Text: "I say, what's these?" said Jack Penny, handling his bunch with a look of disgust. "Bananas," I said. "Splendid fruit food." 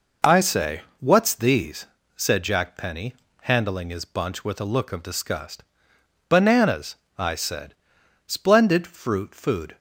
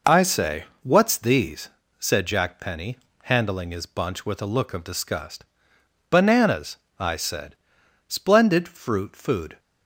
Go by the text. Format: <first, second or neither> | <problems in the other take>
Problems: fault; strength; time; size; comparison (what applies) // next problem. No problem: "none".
neither | none